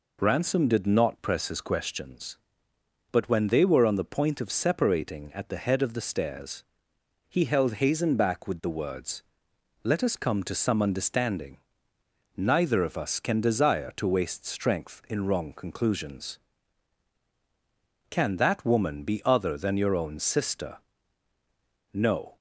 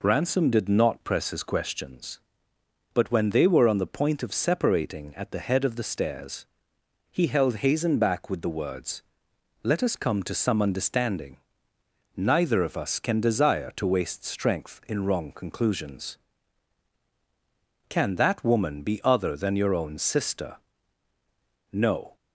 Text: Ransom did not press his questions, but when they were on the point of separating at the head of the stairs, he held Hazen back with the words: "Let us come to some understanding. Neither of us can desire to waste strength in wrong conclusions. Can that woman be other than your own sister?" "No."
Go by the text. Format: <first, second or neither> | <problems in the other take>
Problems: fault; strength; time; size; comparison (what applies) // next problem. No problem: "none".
neither | none